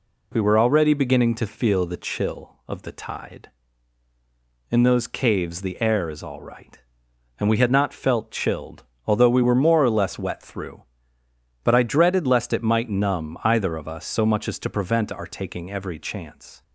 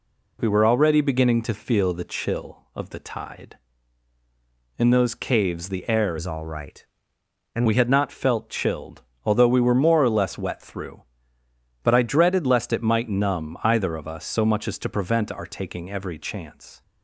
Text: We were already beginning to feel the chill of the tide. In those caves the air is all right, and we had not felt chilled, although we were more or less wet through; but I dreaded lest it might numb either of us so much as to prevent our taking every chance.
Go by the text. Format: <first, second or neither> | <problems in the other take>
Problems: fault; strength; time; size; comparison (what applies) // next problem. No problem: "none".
first | changes voice from "is" to "and"; from 6.1 to 7.6 s; 1.5 s long